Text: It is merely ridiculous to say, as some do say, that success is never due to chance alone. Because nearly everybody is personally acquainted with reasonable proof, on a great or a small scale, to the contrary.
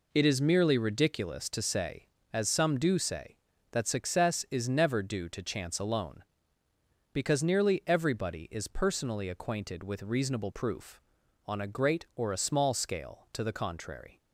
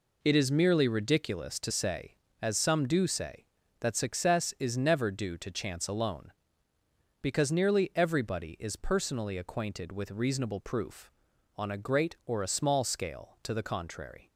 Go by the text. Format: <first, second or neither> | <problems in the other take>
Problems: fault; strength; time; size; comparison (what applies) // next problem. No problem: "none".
neither | none